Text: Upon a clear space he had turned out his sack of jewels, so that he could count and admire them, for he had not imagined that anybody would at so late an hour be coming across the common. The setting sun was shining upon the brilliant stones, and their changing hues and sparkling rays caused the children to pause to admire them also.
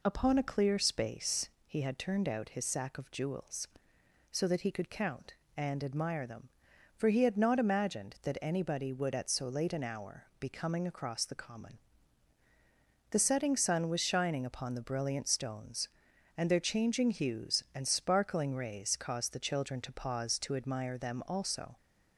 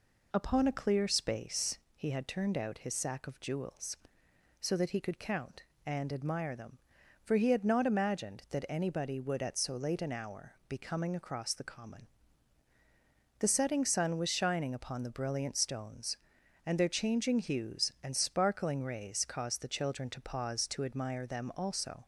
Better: neither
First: pauses between "space" and "he"; slight; at 1.4 s; 0.16 s long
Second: pauses between "space" and "he"; slight; at 1.7 s; 0.16 s long

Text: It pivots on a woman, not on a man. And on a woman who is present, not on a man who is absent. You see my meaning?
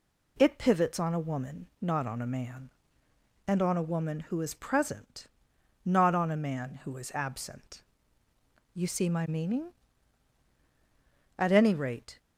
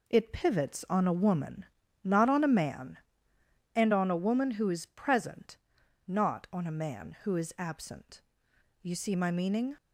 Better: second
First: goes on to say "At any rate"; noticeable; from 11.3 s on; 0.82 s long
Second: none

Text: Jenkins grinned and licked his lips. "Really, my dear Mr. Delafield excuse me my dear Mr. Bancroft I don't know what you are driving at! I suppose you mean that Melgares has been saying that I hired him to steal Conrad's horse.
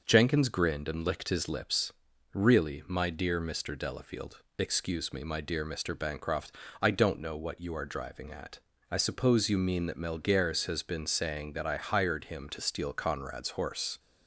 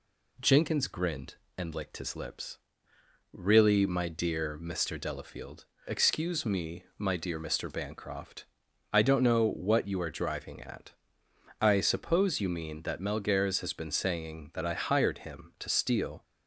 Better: first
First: pauses between "Delafield" and "excuse"; slight; at 4.4 s; 0.18 s long // pauses between "Bancroft" and "I"; slight; at 6.5 s; 0.30 s long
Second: pauses between "Delafield" and "excuse"; slight; at 5.6 s; 0.22 s long // pauses between "me" and "my"; slight; at 6.8 s; 0.16 s long // pauses between "Bancroft" and "I"; noticeable; at 8.4 s; 0.48 s long // stops before "Conrad's horse"; at 16.2 s

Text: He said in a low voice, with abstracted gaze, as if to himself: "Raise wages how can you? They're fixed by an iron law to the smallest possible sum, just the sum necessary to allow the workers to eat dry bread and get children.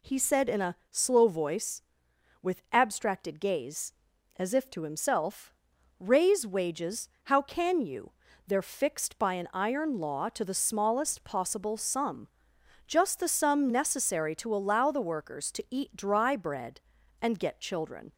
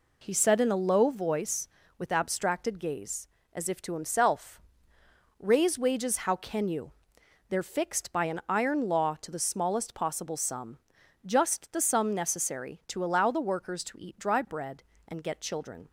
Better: second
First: says "slow" for "low"; at 0.9 s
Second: none

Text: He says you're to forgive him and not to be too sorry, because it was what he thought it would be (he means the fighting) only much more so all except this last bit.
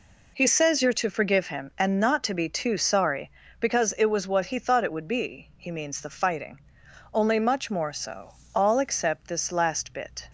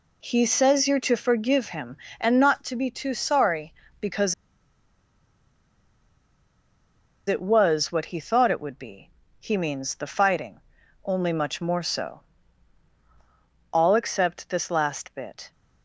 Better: first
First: pauses between "so" and "all"; slight; at 8.3 s; 0.22 s long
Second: pauses between "because" and "it"; strong; at 4.3 s; 2.9 s long // pauses between "so" and "all"; strong; at 12.2 s; 1.5 s long

